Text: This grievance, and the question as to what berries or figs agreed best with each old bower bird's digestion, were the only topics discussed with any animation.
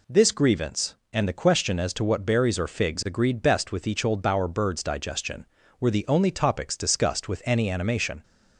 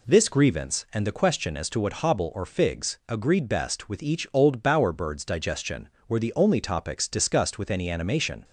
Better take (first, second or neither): first